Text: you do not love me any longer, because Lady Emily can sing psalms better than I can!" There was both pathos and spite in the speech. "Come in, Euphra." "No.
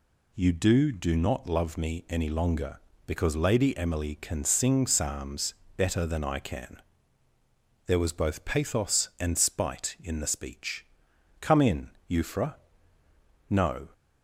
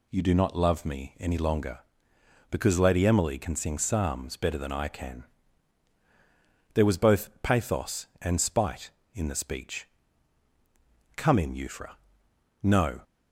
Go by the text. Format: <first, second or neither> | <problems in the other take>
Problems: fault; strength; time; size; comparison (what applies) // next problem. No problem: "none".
second | says "do" twice; at 0.9 s // pauses between "psalms" and "better"; slight; at 5.5 s; 0.22 s long